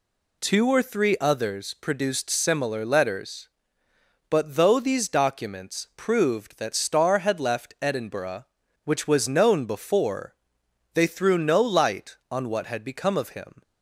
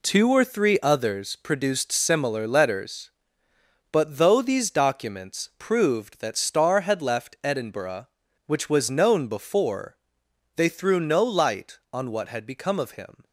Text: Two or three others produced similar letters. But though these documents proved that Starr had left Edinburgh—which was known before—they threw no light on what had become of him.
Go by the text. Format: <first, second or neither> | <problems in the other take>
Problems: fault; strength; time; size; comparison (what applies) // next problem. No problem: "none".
first | gets quieter; strong; throughout; 9.5 dB